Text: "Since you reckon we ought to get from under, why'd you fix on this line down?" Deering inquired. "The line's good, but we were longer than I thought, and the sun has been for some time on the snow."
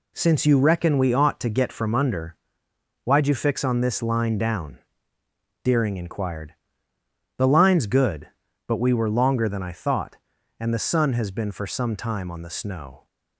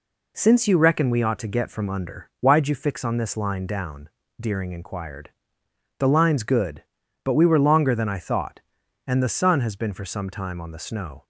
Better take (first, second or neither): neither